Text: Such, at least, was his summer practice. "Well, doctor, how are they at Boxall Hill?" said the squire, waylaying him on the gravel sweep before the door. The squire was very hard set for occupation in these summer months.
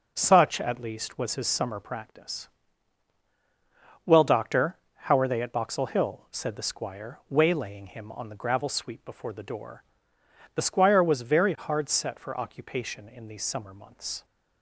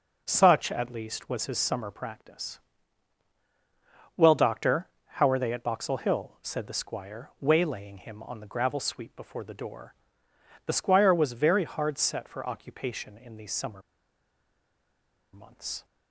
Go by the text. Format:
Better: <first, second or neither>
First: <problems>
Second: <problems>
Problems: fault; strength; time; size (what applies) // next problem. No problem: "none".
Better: first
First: none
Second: pauses between "summer" and "months"; strong; at 13.8 s; 1.5 s long